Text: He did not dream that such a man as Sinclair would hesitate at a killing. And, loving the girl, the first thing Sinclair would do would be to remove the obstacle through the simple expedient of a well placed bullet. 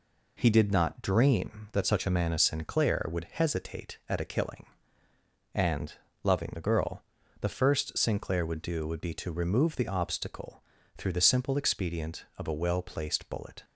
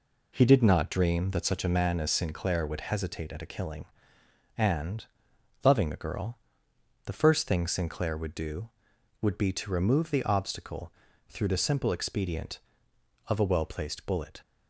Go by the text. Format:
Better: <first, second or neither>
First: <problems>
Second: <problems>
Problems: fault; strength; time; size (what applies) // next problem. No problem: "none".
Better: second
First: skips "thing"; at 7.9 s // pauses between "obstacle" and "through"; slight; at 10.6 s; 0.34 s long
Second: pauses between "obstacle" and "through"; at 10.9 s; 0.38 s long